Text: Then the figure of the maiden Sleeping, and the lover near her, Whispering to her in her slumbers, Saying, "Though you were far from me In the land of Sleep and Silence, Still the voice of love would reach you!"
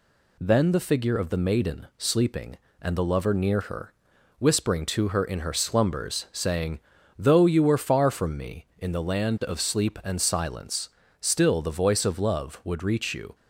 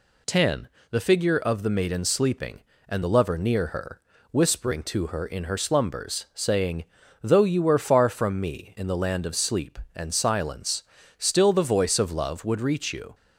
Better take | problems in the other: first | says "Ten" for "Then"; at 0.2 s

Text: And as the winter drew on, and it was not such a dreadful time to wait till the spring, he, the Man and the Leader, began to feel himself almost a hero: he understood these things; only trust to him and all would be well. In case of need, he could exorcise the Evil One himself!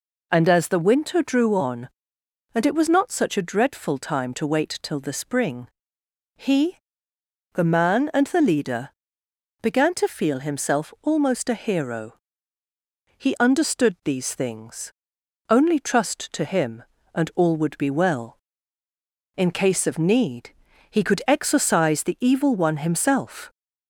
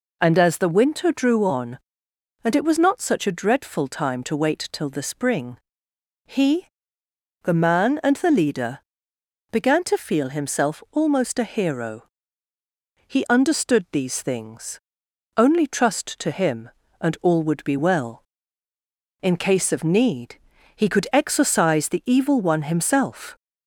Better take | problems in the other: neither | none

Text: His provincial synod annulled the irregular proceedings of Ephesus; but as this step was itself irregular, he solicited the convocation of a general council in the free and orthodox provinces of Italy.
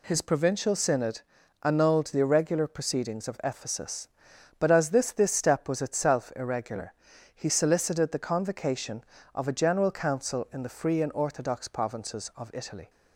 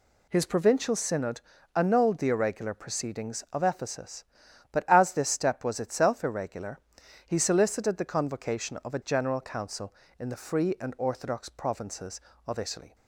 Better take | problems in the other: second | pauses between "synod" and "annulled"; at 1.2 s; 0.42 s long; slight in the second // says "this" twice; at 5.1 s

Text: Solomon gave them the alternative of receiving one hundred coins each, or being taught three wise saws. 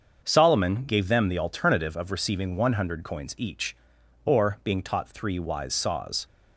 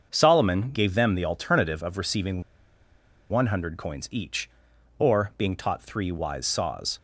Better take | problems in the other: first | starts louder than the rest; until 1.1 s; 6.5 dB; also in the first // pauses between "receiving" and "one"; noticeable; at 2.4 s; 0.88 s long

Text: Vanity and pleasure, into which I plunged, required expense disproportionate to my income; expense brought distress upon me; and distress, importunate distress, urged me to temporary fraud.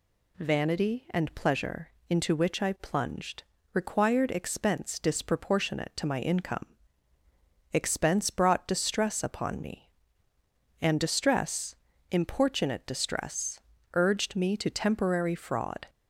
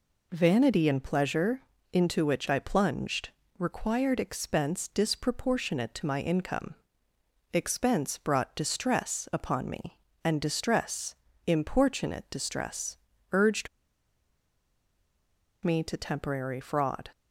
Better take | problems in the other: first | pauses between "urged" and "me"; strong; at 13.6 s; 1.9 s long

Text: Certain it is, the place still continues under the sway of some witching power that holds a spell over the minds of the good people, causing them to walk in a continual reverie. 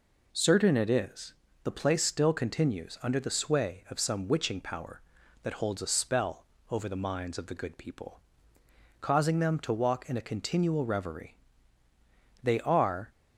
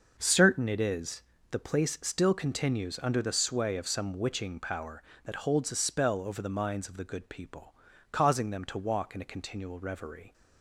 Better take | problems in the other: second | pauses between "spell" and "over"; slight; at 6.4 s; 0.24 s long // goes on to say "They are"; noticeable; from 12.4 s on; 0.68 s long

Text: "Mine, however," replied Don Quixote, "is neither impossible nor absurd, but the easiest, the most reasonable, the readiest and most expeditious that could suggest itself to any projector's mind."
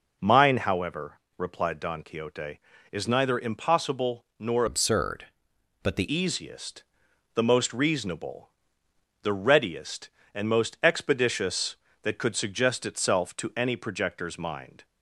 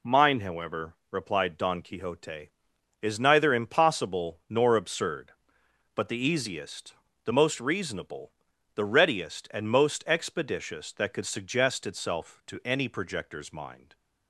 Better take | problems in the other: second | changes voice from "absurd" to "the"; from 4.6 to 6.0 s; 1.4 s long

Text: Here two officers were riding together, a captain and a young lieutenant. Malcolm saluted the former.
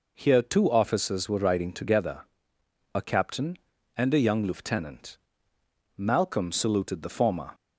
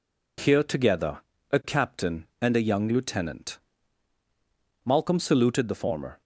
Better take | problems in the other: first | skips "two officers were riding"; at 0.6 s

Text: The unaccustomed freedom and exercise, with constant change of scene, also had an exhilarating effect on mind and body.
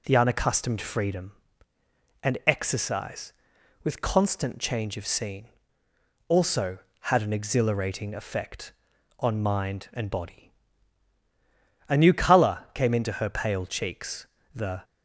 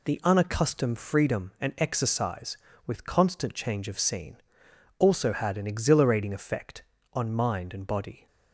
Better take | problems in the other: second | goes on to say "A new colour came into her pale cheeks the"; strong; from 11.8 s on; 2.9 s long

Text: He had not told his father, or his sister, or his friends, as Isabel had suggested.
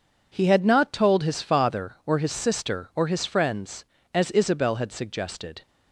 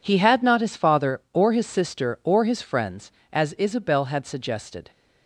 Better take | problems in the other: first | skips "told"; at 0.6 s

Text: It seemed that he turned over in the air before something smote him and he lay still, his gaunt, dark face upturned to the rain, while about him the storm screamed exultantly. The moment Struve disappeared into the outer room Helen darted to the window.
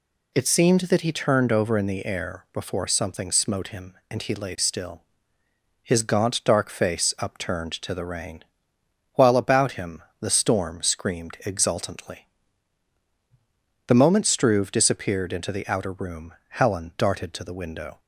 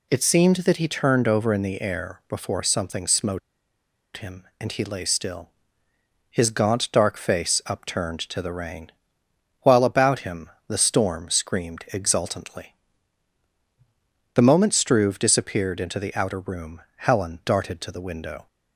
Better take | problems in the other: first | pauses between "smote" and "him"; noticeable; at 3.3 s; 0.76 s long // pauses between "him" and "the"; slight; at 10.5 s; 0.16 s long; slight in the first // pauses between "room" and "Helen"; slight; at 16.8 s; 0.16 s long; slight in the first

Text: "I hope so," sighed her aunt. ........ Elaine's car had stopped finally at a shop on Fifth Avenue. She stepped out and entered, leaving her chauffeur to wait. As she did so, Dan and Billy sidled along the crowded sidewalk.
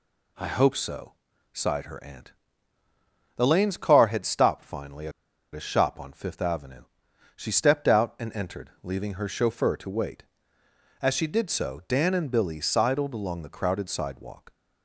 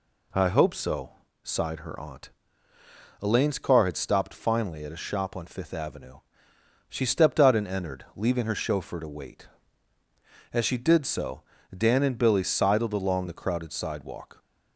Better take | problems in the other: second | pauses between "at" and "a"; at 5.1 s; 0.43 s long

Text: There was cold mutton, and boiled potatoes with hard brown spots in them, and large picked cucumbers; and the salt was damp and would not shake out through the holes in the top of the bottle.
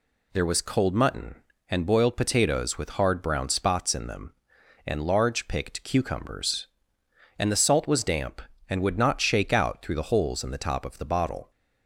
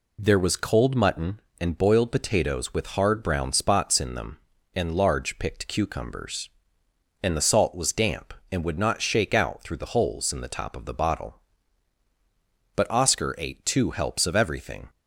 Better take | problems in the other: first | goes on to say "But Oscar ate two helps of everything"; strong; from 12.7 s on; 2.1 s long

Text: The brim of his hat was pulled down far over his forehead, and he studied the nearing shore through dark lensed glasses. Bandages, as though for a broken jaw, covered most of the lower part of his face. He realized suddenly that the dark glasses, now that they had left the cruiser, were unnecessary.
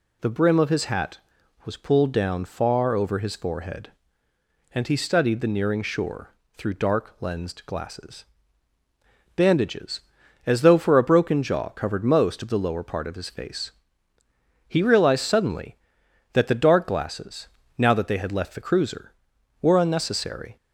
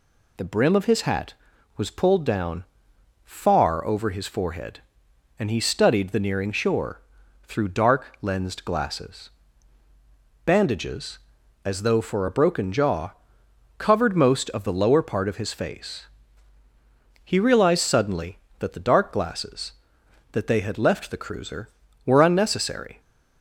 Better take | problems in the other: first | pauses between "down" and "far"; noticeable; at 2.6 s; 0.60 s long // pauses between "shore" and "through"; at 7.0 s; 0.42 s long; slight in the first // skips "now"; at 20.0 s

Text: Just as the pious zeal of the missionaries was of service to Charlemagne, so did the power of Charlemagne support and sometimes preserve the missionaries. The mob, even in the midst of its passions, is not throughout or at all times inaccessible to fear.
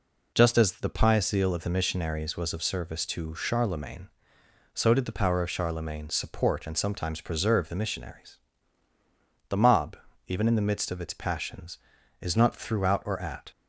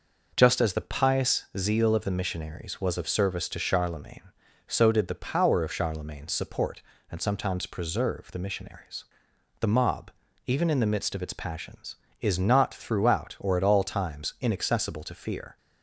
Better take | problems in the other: second | stops before "all times inaccessible to fear"; at 13.5 s

